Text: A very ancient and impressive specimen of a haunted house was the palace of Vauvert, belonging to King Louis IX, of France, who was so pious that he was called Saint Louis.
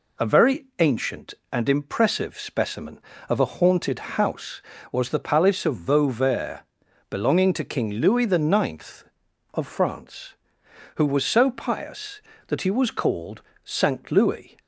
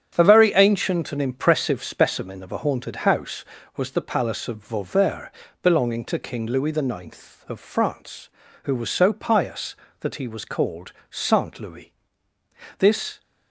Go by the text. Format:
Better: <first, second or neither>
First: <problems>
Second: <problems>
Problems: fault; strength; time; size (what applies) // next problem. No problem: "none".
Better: first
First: pauses between "called" and "Saint"; slight; at 13.4 s; 0.24 s long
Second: starts louder than the rest; strong; until 1.1 s; 8.5 dB // pauses between "called" and "Saint"; slight; at 10.9 s; 0.18 s long // goes on to say "This"; slight; from 12.7 s on; 0.42 s long